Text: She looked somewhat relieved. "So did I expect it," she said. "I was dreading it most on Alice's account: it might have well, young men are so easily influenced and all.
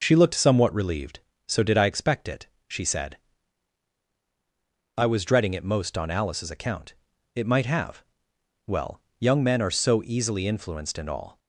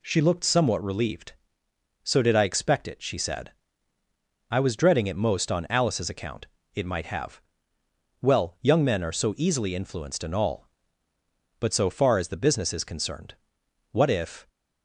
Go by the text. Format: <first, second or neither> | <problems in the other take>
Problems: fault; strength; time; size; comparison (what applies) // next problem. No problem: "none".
first | pauses between "have" and "well"; noticeable; at 7.3 s; 0.80 s long; noticeable in the first // goes on to say "But so far as the business is concerned what if"; strong; from 11.5 s on; 2.9 s long